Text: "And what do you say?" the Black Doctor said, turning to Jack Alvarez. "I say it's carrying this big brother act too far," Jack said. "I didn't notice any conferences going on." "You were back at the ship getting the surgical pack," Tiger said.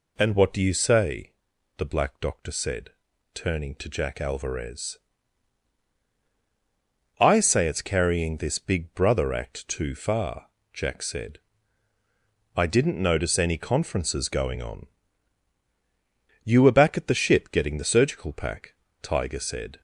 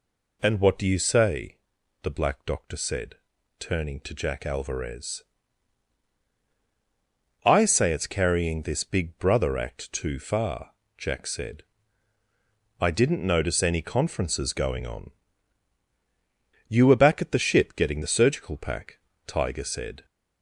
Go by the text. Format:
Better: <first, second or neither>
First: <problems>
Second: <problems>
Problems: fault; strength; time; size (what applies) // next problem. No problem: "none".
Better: neither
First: none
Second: none